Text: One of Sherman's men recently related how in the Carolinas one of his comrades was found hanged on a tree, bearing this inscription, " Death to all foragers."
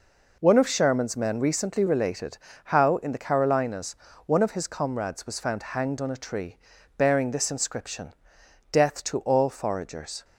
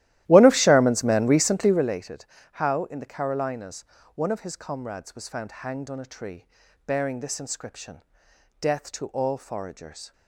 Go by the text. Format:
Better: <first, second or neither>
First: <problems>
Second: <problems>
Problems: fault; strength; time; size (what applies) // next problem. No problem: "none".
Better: first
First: pauses between "related" and "how"; slight; at 2.3 s; 0.28 s long // pauses between "Carolinas" and "one"; slight; at 3.9 s; 0.30 s long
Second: starts louder than the rest; strong; until 2.0 s; 14.5 dB // pauses between "related" and "how"; slight; at 2.2 s; 0.28 s long // pauses between "Carolinas" and "one"; slight; at 3.8 s; 0.30 s long